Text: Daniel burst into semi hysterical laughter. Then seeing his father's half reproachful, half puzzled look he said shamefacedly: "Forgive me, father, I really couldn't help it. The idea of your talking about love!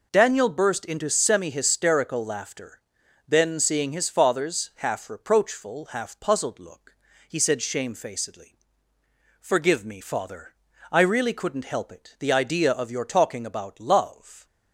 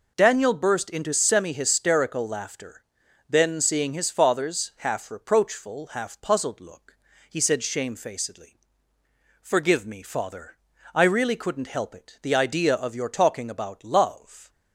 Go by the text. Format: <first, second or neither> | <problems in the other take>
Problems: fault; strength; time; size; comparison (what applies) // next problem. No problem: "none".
neither | pauses between "look" and "he"; slight; the same in both